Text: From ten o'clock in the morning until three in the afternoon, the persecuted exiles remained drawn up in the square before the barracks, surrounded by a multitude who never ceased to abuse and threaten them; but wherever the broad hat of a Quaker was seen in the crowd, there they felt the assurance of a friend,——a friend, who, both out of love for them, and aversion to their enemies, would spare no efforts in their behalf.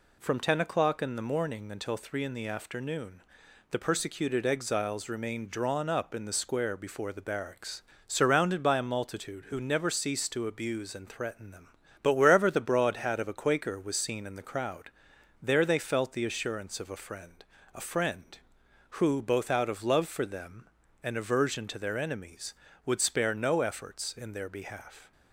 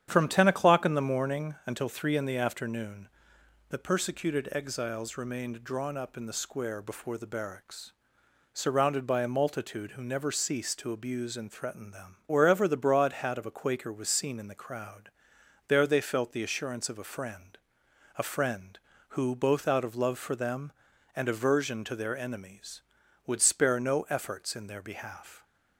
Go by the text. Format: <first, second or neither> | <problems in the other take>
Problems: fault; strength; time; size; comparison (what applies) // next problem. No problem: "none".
first | starts louder than the rest; strong; until 1.1 s; 9 dB // skips "but"; at 12.2 s